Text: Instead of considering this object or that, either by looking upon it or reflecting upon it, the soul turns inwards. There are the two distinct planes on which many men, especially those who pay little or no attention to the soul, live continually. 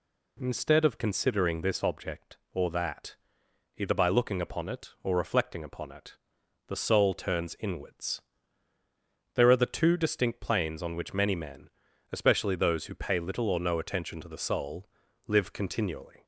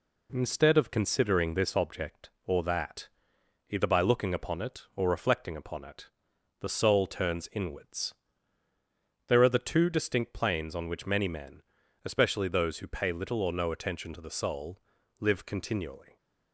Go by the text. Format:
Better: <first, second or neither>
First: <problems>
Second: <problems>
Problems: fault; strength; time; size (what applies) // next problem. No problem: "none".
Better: first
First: none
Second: gets quieter; slight; throughout; 3.5 dB